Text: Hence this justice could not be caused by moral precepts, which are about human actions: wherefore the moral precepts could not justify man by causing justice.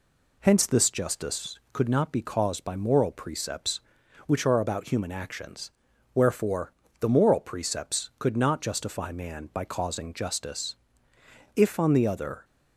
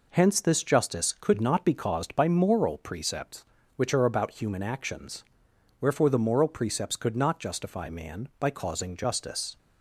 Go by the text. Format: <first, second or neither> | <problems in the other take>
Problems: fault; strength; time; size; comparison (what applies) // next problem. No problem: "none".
second | pauses between "wherefore" and "the"; slight; at 6.7 s; 0.28 s long // goes on to say "If on the other"; noticeable; from 11.5 s on; 0.88 s long